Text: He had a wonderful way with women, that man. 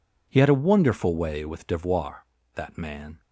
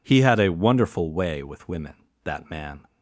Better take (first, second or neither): second